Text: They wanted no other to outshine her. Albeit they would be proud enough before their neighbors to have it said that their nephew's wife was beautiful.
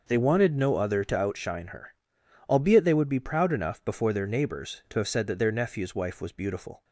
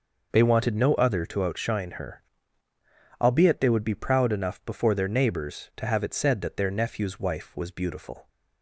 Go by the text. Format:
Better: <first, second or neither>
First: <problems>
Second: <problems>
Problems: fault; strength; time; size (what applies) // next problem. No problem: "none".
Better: second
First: skips "it"; at 5.0 s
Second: none